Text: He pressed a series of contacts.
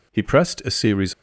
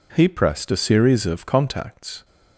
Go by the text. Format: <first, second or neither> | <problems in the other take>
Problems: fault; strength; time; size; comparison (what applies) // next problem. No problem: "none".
second | stops before "of contacts"; at 1.1 s